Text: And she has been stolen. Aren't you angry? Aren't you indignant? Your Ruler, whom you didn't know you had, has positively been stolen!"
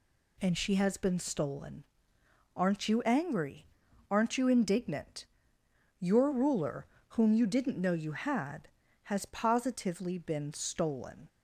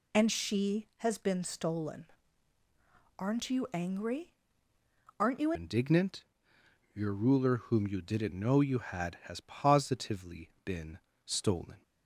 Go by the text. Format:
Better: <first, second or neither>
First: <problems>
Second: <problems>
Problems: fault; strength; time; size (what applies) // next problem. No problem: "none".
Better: first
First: none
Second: changes voice at "indignant"; from 5.5 s on; 6.3 s long // pauses between "been" and "stolen"; slight; at 10.9 s; 0.26 s long